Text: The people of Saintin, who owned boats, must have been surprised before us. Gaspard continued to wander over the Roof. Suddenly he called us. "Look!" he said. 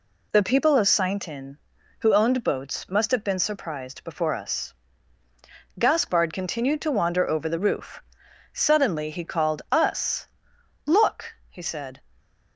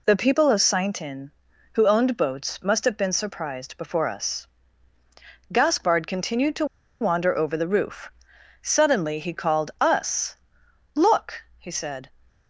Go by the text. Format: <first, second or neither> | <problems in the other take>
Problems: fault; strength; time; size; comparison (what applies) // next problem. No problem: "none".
first | pauses between "to" and "wander"; slight; at 6.6 s; 0.34 s long